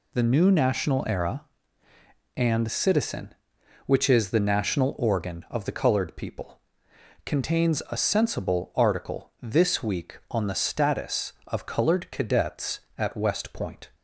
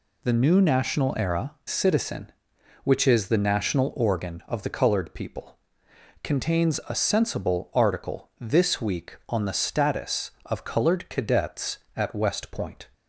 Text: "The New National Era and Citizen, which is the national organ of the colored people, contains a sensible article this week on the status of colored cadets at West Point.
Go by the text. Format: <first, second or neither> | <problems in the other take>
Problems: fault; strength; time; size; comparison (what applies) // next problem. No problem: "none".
first | skips "and"; at 1.6 s